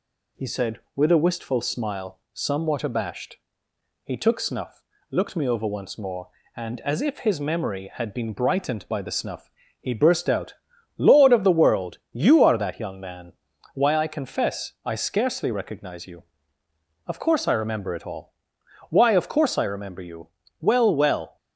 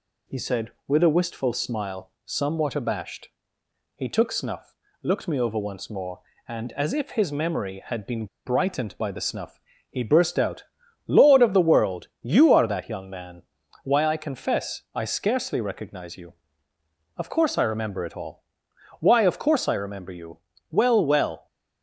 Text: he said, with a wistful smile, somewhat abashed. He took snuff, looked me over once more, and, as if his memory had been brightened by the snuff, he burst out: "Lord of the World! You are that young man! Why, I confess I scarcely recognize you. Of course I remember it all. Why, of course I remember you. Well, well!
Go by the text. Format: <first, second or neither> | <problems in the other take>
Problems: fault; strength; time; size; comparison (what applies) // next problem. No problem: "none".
first | pauses between "been" and "brightened"; slight; at 8.2 s; 0.19 s long